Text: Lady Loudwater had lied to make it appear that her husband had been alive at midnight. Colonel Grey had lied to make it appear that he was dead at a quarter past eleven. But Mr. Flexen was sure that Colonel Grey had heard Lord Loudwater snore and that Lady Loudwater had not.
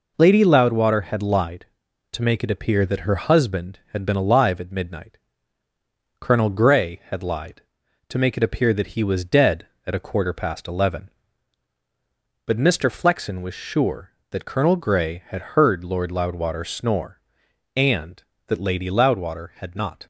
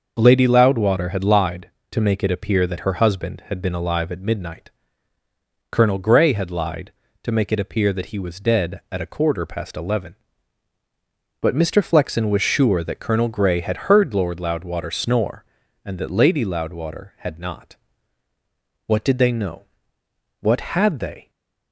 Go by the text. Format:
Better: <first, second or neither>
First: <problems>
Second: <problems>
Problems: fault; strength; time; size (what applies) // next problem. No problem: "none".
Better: first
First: none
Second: starts louder than the rest; until 1.1 s; 6 dB // goes on to say "What did they know What had they"; strong; from 18.8 s on; 2.4 s long // stays silent after the last word; slight; from 21.2 s on; 0.5 s long